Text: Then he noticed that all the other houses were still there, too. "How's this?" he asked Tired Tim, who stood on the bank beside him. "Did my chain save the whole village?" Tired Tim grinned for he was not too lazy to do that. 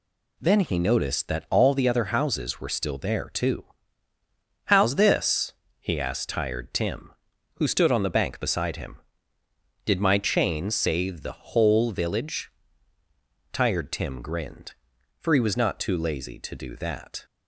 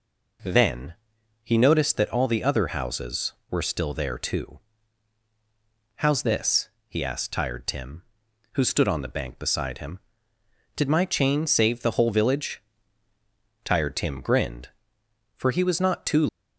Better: first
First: none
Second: pauses between "Then" and "he"; noticeable; at 0.9 s; 0.48 s long // stops before "lazy to do that"; at 16.2 s

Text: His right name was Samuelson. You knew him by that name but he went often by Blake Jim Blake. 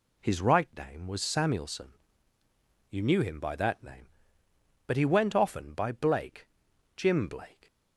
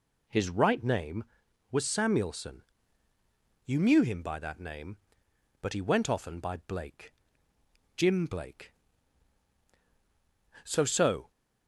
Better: first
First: pauses between "Blake" and "Jim"; noticeable; at 6.4 s; 0.48 s long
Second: pauses between "Blake" and "Jim"; noticeable; at 7.1 s; 0.84 s long // goes on to say "So so"; noticeable; from 10.6 s on; 0.66 s long

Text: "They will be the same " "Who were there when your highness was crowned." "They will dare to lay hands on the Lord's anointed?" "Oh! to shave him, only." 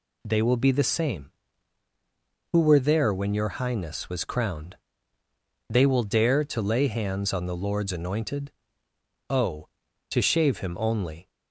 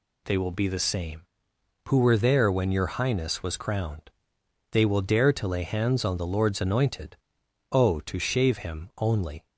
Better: neither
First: none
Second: none

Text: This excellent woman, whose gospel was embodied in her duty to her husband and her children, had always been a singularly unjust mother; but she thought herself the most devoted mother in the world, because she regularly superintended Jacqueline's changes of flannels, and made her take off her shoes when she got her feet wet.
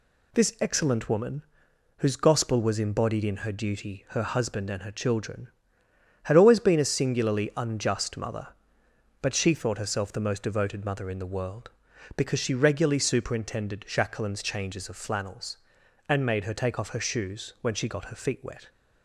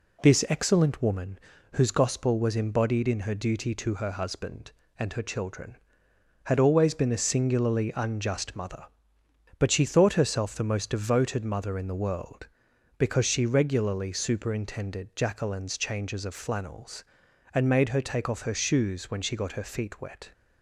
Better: second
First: skips "to"; at 4.0 s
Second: none

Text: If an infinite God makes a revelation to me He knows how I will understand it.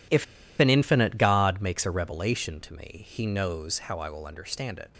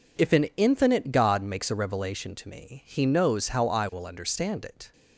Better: second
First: pauses between "If" and "an"; slight; at 0.2 s; 0.34 s long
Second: none

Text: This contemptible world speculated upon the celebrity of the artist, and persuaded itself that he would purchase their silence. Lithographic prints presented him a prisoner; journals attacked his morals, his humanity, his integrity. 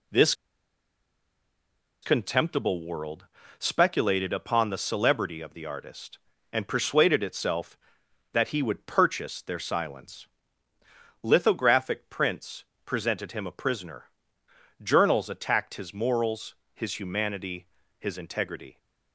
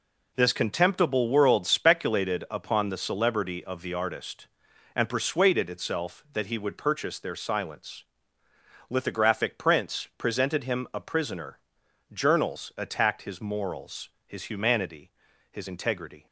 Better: second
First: pauses between "This" and "contemptible"; strong; at 0.3 s; 1.6 s long // pauses between "world" and "speculated"; slight; at 3.2 s; 0.34 s long // pauses between "prints" and "presented"; slight; at 12.6 s; 0.22 s long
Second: none

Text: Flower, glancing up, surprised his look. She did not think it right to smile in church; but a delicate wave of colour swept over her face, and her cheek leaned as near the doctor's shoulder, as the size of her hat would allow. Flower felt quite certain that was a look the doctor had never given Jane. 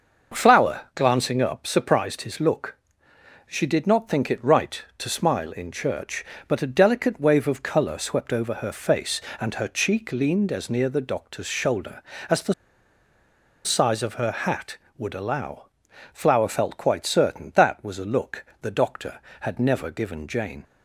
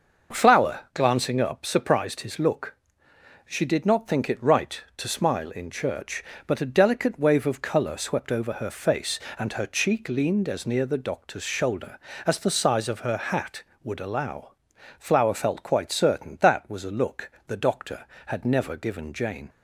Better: second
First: starts louder than the rest; until 1.4 s; 6 dB // pauses between "the" and "size"; at 12.5 s; 1.1 s long // pauses between "look" and "the"; slight; at 18.4 s; 0.16 s long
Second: starts louder than the rest; until 1.4 s; 6 dB // pauses between "look" and "the"; slight; at 17.3 s; 0.16 s long

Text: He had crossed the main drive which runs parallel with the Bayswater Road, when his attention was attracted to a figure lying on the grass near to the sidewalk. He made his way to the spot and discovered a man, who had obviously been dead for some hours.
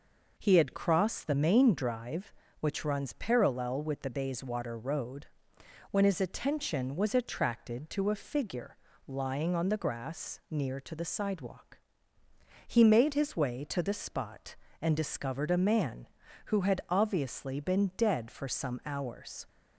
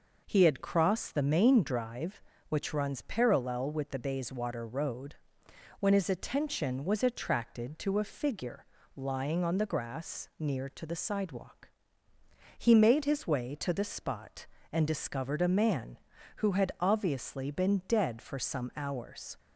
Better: neither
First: pauses between "figure" and "lying"; slight; at 8.7 s; 0.30 s long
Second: pauses between "figure" and "lying"; slight; at 8.6 s; 0.30 s long

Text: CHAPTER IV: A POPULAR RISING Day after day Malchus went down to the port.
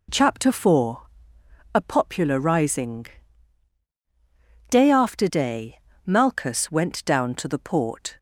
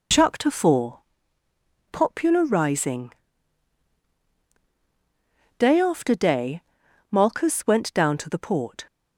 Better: first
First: pauses between "RISING" and "Day"; strong; at 3.0 s; 1.6 s long // pauses between "day" and "Malchus"; slight; at 5.7 s; 0.26 s long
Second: skips "A"; at 1.4 s // pauses between "RISING" and "Day"; strong; at 3.1 s; 2.4 s long // pauses between "day" and "Malchus"; noticeable; at 6.6 s; 0.48 s long

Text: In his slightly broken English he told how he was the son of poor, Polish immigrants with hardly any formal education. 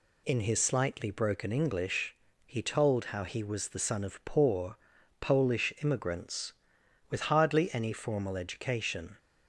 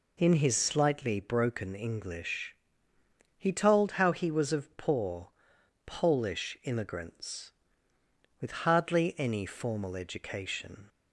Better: first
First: pauses between "English" and "he"; slight; at 2.1 s; 0.30 s long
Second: pauses between "English" and "he"; noticeable; at 2.5 s; 0.80 s long // skips "the son"; at 4.5 s

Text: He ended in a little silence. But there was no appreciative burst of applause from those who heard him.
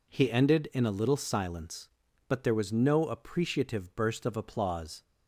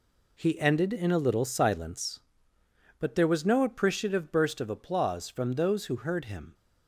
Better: second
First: stops before "from those who heard him"; at 5.0 s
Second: none

